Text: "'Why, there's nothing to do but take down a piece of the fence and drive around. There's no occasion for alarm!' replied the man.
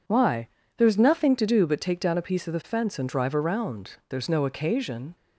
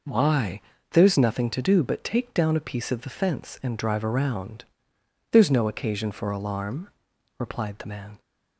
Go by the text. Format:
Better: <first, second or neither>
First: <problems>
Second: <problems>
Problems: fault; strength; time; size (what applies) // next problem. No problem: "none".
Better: second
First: stops before "for alarm replied the man"; at 5.1 s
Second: none